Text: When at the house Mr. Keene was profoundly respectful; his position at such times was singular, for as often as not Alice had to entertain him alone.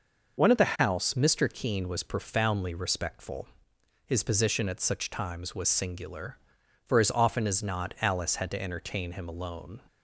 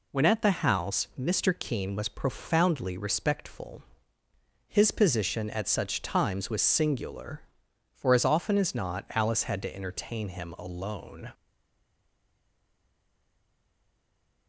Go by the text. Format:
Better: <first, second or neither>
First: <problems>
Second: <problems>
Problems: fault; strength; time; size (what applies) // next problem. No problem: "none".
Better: first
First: none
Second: stays silent after the last word; strong; from 11.3 s on; 3.1 s long